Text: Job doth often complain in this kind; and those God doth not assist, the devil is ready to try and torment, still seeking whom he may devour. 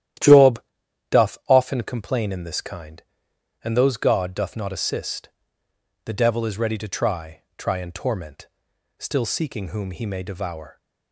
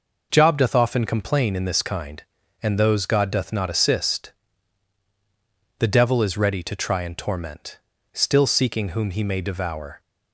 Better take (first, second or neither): second